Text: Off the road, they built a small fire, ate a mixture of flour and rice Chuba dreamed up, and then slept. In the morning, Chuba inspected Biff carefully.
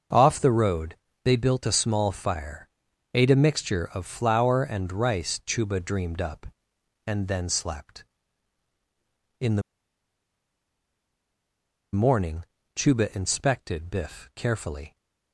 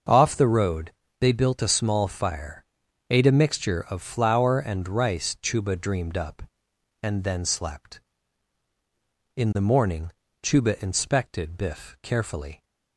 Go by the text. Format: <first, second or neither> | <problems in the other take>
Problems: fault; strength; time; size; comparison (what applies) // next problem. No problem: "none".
second | starts louder than the rest; until 1.4 s; 6 dB; also in the second // pauses between "the" and "morning"; strong; at 9.6 s; 2.3 s long